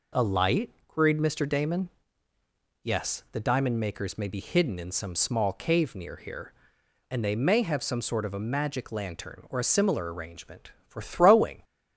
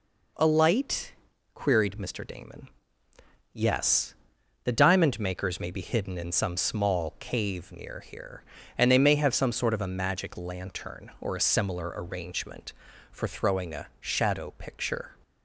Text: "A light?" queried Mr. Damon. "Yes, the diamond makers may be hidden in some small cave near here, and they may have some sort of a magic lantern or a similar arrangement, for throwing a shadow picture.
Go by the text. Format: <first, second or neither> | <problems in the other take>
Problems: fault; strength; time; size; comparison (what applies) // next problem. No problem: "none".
second | stops before "a shadow picture"; at 11.6 s